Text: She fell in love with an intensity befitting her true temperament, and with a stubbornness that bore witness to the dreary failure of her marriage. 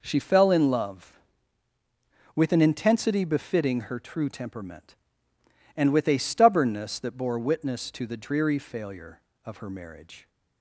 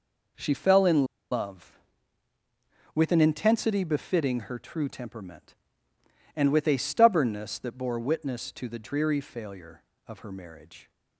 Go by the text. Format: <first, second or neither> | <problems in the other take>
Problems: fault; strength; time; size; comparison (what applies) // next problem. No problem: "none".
first | pauses between "in" and "love"; slight; at 1.0 s; 0.25 s long